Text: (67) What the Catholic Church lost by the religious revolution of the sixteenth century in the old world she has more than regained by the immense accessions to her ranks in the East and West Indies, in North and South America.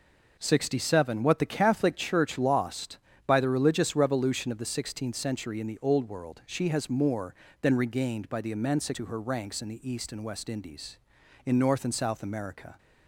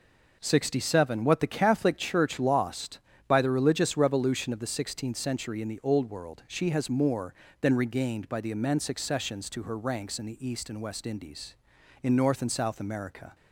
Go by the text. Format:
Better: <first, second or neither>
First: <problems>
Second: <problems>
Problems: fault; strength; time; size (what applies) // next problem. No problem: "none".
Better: second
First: skips "accessions"; at 8.9 s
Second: none